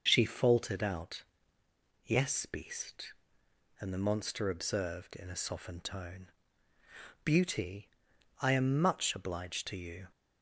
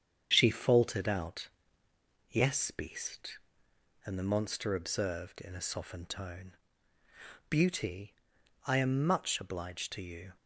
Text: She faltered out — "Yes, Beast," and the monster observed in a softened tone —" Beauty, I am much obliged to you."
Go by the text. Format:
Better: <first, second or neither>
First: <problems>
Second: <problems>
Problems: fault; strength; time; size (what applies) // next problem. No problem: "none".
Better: first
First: none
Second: gets quieter; noticeable; throughout; 4 dB